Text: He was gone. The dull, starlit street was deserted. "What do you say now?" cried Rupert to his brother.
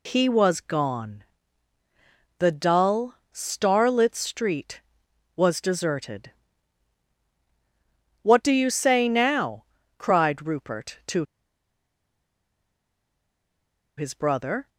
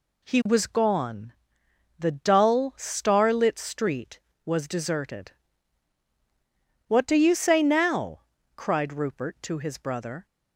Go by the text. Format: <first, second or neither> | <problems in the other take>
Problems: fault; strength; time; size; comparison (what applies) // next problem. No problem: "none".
second | pauses between "to" and "his"; strong; at 11.2 s; 2.7 s long